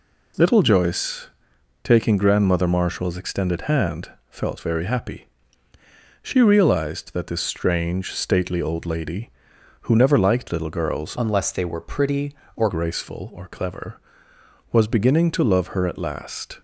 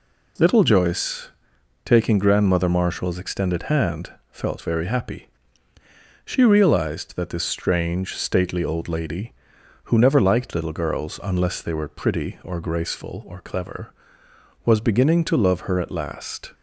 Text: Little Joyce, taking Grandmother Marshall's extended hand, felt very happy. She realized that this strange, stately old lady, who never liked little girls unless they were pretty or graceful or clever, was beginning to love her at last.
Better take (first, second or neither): second